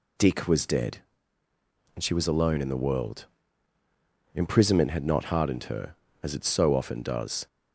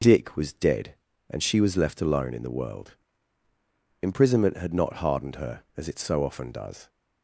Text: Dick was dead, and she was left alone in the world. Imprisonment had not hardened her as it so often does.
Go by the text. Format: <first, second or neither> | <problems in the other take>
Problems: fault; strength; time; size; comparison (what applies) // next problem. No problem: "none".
second | skips "left"; at 2.2 s